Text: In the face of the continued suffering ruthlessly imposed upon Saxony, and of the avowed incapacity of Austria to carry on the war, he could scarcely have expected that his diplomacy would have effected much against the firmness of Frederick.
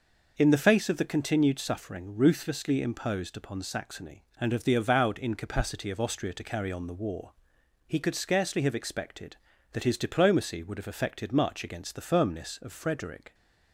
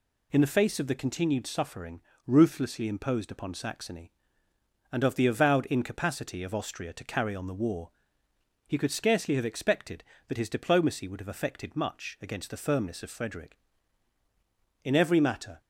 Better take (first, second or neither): first